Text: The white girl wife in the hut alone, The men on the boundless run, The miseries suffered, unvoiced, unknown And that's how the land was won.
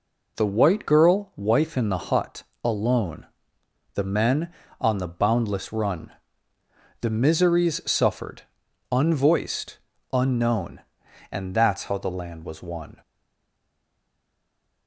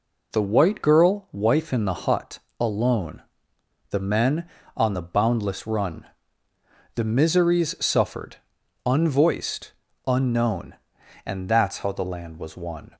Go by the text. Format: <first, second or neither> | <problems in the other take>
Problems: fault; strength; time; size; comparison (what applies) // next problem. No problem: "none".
second | pauses between "hut" and "alone"; slight; at 2.4 s; 0.18 s long; slight in the second // stays silent after the last word; noticeable; from 13.0 s on; 1.8 s long